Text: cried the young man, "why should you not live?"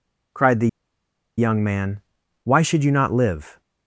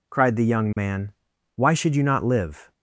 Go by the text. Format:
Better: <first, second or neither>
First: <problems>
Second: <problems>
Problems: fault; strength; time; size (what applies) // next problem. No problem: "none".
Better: second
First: pauses between "the" and "young"; noticeable; at 0.6 s; 0.69 s long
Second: none